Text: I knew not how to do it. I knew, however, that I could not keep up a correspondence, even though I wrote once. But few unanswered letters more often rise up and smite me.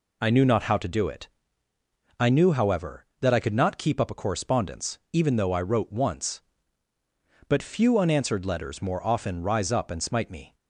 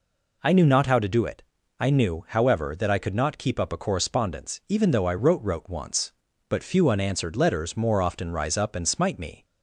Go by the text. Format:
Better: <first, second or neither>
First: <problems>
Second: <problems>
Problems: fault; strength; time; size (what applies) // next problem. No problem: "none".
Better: first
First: none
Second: says "wrote" twice; at 5.4 s